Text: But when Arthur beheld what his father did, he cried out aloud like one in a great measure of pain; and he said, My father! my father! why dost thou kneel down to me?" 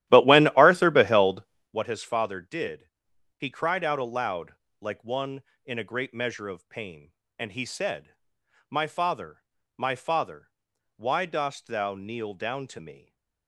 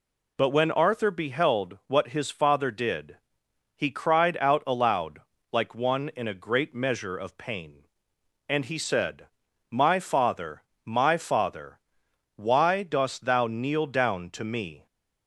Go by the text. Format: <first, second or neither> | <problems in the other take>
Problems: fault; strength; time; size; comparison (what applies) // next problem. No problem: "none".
second | starts louder than the rest; strong; until 1.8 s; 13.5 dB // pauses between "beheld" and "what"; slight; at 1.4 s; 0.28 s long // pauses between "aloud" and "like"; slight; at 4.5 s; 0.24 s long; slight in the second // stays silent after the last word; slight; from 12.9 s on; 0.5 s long